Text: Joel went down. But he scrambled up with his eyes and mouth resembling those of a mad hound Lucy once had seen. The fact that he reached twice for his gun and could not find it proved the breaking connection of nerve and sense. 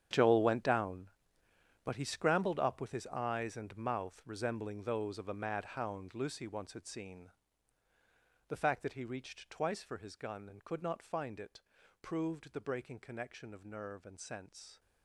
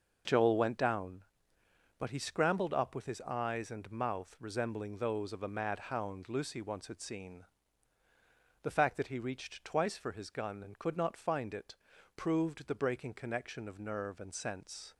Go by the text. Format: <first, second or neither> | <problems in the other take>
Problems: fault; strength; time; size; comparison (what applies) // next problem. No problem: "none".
second | gets quieter; strong; throughout; 15 dB // pauses between "it" and "proved"; at 11.6 s; 0.40 s long; also in the second